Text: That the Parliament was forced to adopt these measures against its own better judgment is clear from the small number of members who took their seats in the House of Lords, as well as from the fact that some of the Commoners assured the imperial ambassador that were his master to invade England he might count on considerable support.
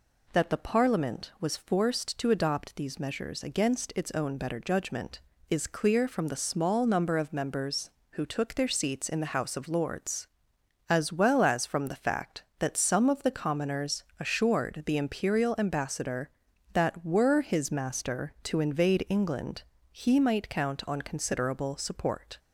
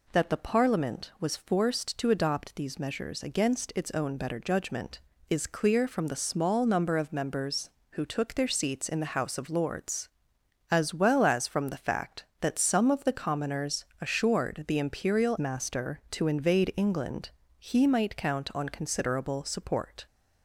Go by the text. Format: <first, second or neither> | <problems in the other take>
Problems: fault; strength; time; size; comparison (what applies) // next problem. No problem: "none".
first | pauses between "Commoners" and "assured"; slight; at 13.8 s; 0.16 s long; slight in the first // skips "ambassador that were his"; at 15.3 s // pauses between "England" and "he"; slight; at 17.2 s; 0.30 s long; slight in the first